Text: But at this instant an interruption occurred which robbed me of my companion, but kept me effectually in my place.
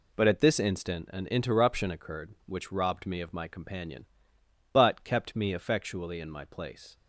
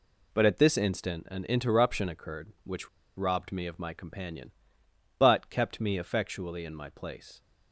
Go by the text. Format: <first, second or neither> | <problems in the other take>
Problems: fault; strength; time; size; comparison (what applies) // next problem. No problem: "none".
first | pauses between "which" and "robbed"; slight; at 2.8 s; 0.28 s long